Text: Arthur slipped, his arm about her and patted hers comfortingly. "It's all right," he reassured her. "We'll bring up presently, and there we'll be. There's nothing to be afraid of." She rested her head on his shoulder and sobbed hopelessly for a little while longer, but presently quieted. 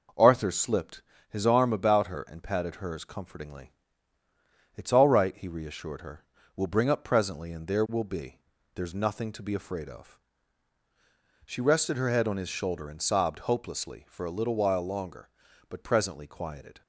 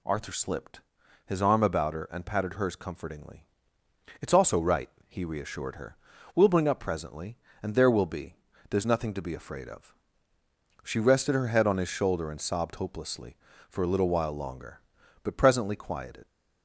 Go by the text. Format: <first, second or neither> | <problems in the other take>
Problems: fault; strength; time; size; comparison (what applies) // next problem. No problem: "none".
first | says "also" for "all"; at 4.3 s